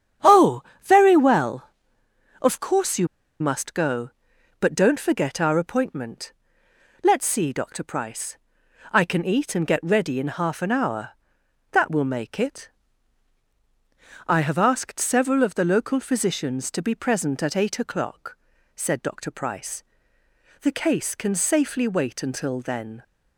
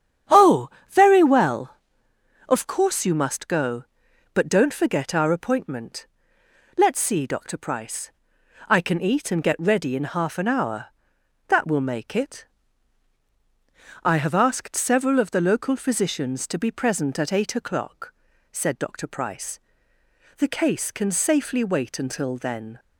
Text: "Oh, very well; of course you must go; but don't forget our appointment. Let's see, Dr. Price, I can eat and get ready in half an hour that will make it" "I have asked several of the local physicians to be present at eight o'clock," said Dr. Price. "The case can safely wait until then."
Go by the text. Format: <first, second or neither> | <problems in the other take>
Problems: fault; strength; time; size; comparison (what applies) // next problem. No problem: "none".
second | starts louder than the rest; strong; until 1.4 s; 9 dB; strong in the second // pauses between "you" and "must"; slight; at 3.0 s; 0.33 s long // pauses between "it" and "I"; strong; at 12.6 s; 1.5 s long; strong in the second